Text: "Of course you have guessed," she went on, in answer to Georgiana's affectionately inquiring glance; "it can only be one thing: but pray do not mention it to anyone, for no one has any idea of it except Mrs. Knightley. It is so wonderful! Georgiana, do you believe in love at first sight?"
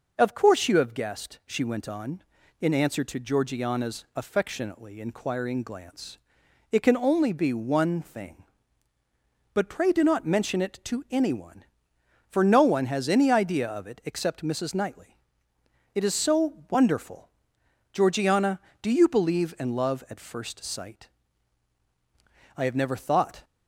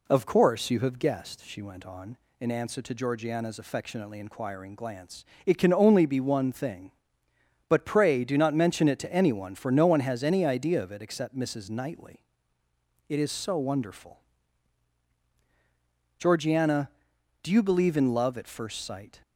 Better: second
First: goes on to say "I have never thought"; noticeable; from 22.5 s on; 0.90 s long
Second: none

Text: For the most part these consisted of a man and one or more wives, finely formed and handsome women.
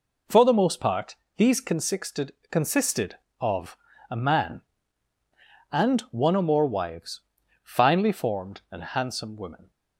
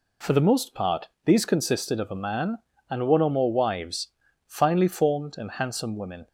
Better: second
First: pauses between "part" and "these"; slight; at 1.1 s; 0.20 s long // says "consisted" twice; at 2.5 s // pauses between "of" and "a"; slight; at 3.7 s; 0.34 s long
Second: pauses between "part" and "these"; slight; at 1.0 s; 0.18 s long

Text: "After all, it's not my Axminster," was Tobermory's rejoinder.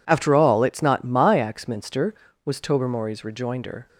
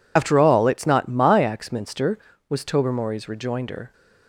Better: first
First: none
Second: loses the start of "After"; at 0.1 s; 45 ms

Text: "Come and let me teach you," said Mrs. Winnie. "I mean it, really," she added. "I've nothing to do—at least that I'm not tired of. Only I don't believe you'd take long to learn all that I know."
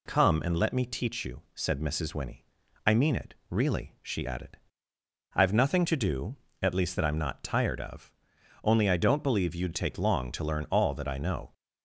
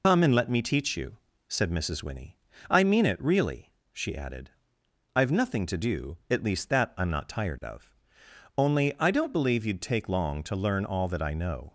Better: first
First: none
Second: loses the start of "Come"; at 0.0 s; 95 ms

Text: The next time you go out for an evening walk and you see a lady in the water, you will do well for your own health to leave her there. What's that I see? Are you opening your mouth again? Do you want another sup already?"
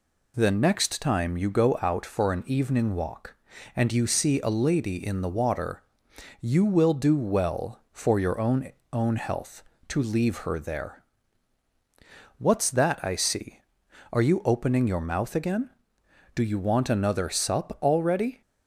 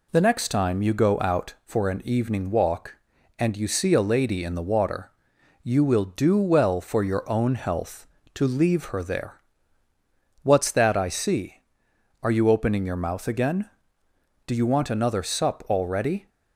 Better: second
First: says "own" twice; at 8.9 s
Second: none

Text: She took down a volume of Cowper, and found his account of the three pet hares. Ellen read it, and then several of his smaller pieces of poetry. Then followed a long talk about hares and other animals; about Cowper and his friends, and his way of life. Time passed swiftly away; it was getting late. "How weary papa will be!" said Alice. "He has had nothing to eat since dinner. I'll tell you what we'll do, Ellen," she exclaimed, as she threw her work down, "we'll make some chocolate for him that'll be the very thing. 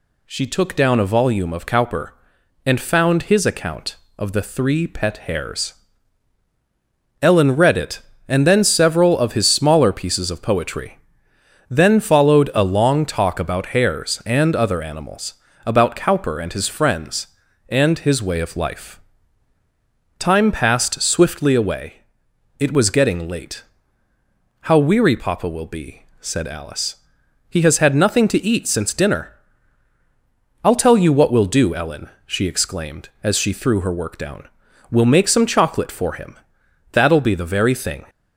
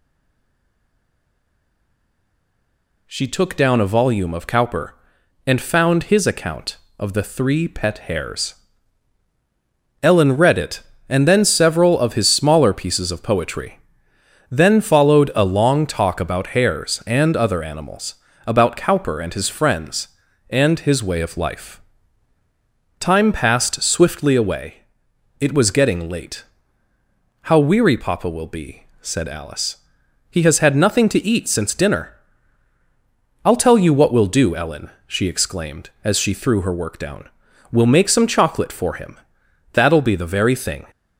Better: first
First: pauses between "him" and "that'll"; noticeable; at 36.3 s; 0.56 s long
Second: stays silent before the first word; strong; until 3.0 s; 3.0 s long // pauses between "him" and "that'll"; noticeable; at 39.1 s; 0.56 s long

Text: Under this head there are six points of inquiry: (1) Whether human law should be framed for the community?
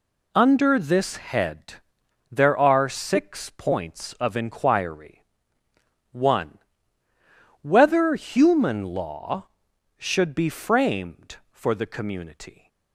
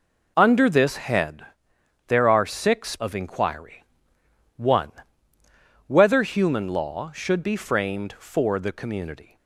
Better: first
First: pauses between "head" and "there"; noticeable; at 1.7 s; 0.58 s long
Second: pauses between "head" and "there"; noticeable; at 1.4 s; 0.62 s long // skips "points"; at 2.9 s

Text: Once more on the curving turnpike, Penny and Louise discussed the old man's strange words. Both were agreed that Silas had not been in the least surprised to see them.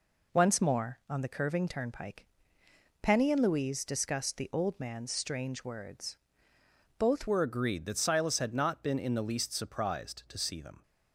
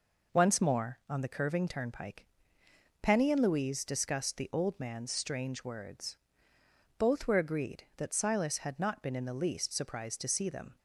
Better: second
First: changes voice at "were"; from 7.2 s on; 3.6 s long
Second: none

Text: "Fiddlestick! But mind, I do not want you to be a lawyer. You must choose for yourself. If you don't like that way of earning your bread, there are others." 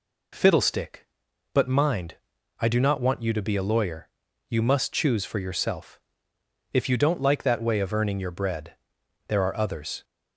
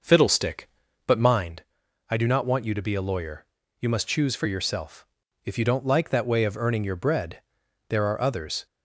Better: first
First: none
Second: starts louder than the rest; noticeable; until 1.6 s; 6 dB

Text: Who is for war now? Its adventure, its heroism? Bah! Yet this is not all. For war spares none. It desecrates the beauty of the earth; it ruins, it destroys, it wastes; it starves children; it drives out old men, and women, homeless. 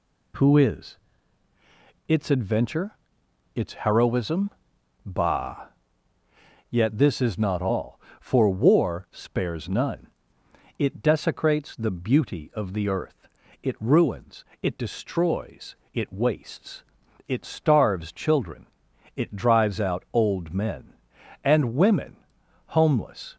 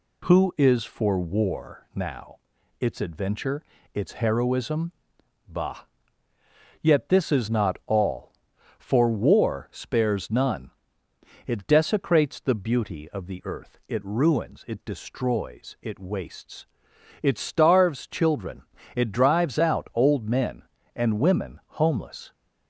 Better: second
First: skips "for war now"; at 1.5 s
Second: none

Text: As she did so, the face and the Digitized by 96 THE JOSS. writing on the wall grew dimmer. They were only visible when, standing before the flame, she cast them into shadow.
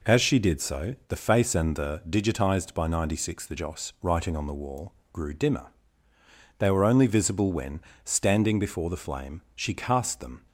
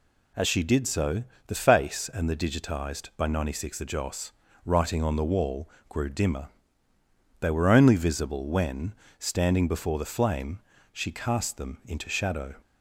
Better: second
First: pauses between "wall" and "grew"; slight; at 4.9 s; 0.18 s long // stops before "into shadow"; at 10.4 s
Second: pauses between "wall" and "grew"; slight; at 5.6 s; 0.18 s long

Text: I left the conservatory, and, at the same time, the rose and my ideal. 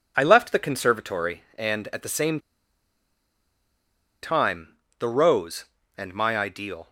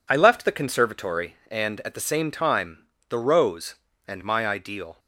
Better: second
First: pauses between "same" and "time"; strong; at 2.3 s; 1.8 s long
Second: none

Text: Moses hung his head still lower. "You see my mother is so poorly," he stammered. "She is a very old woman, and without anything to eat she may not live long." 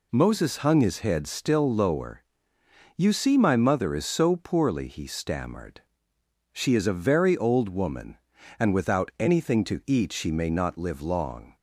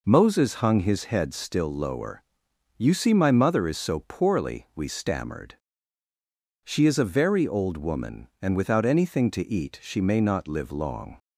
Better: first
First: none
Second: says "we" for "he"; at 4.7 s

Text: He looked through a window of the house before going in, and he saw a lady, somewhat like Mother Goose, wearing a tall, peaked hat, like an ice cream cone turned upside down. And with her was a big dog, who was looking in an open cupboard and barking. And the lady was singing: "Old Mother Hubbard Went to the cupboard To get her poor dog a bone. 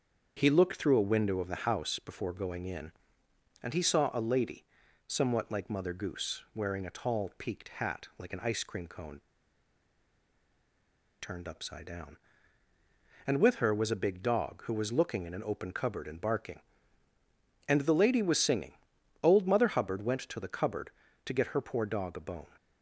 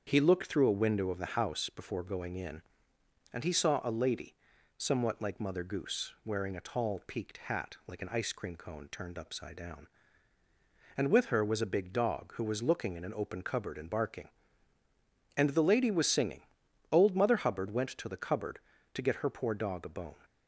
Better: second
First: starts louder than the rest; until 1.3 s; 7 dB // pauses between "cone" and "turned"; strong; at 9.1 s; 2.0 s long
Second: starts louder than the rest; until 1.0 s; 7 dB

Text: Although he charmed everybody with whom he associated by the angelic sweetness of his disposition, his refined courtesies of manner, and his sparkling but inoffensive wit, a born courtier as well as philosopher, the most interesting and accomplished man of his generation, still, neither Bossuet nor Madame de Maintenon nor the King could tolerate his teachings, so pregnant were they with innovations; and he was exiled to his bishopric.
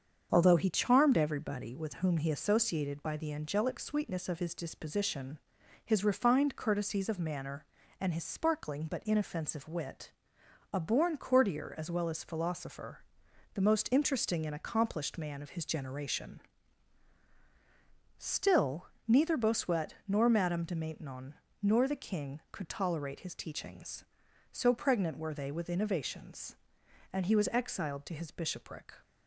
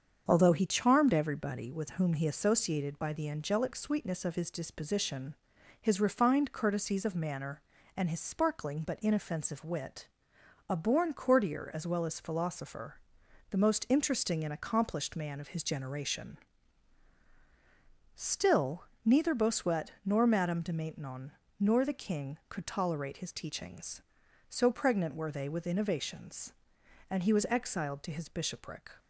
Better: neither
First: starts louder than the rest; strong; until 1.3 s; 7.5 dB // pauses between "Maintenon" and "nor"; slight; at 21.3 s; 0.30 s long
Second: starts louder than the rest; strong; until 1.2 s; 7.5 dB // pauses between "Maintenon" and "nor"; slight; at 21.3 s; 0.30 s long

